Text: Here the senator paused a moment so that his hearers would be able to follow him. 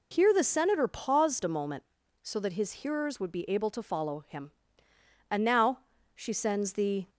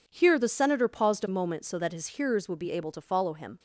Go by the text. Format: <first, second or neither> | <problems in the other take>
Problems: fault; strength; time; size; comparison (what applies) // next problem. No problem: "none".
second | goes on to say "And now she sends the"; strong; from 5.2 s on; 1.8 s long